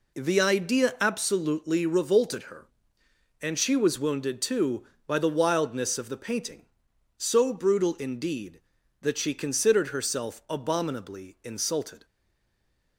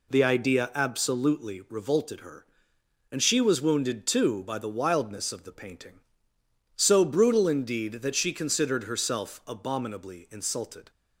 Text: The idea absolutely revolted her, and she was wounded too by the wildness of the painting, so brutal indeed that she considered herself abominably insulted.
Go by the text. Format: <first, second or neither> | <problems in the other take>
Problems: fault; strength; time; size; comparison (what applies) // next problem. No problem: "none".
second | stays silent after the last word; slight; from 12.0 s on; 0.9 s long